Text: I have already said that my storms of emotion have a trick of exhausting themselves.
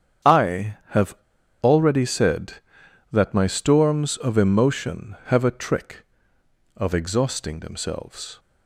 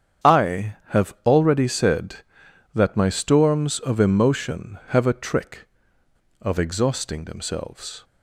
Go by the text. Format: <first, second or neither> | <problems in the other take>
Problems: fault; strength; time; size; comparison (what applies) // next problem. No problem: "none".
second | starts louder than the rest; strong; until 1.8 s; 8.5 dB; strong in the second // pauses between "have" and "already"; noticeable; at 1.1 s; 0.46 s long